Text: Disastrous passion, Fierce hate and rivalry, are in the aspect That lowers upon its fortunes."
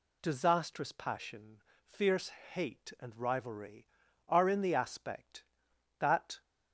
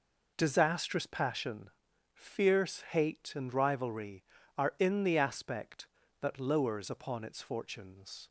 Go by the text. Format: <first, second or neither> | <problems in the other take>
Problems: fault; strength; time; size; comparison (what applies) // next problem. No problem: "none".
second | pauses between "Fierce" and "hate"; slight; at 2.2 s; 0.22 s long // stops before "lowers upon its fortunes"; at 6.4 s